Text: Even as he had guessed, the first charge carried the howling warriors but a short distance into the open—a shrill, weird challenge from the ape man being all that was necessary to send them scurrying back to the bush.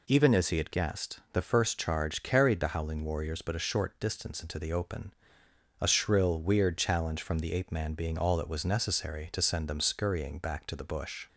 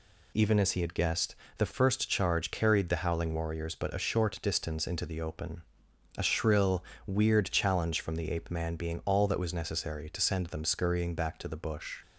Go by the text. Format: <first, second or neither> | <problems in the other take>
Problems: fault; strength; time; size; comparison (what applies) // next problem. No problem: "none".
neither | none